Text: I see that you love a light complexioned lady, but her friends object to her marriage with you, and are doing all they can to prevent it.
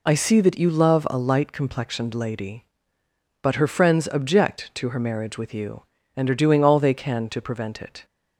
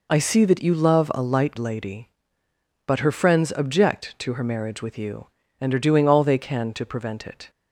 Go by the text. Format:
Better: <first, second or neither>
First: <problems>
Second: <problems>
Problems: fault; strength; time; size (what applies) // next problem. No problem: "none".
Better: first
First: none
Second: skips "complexioned"; at 1.5 s